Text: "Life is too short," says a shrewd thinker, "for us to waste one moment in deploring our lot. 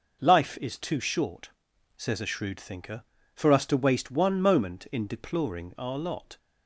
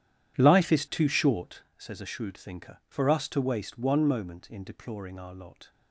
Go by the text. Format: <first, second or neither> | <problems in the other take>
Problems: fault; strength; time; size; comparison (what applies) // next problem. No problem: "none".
first | starts louder than the rest; strong; until 1.7 s; 10.5 dB